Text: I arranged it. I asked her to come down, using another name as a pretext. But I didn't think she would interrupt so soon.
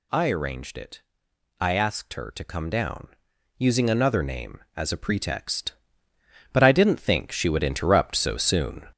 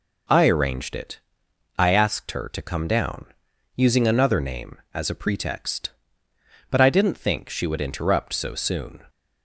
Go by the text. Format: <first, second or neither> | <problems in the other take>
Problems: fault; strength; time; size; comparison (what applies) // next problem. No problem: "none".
second | gets louder; throughout; 6 dB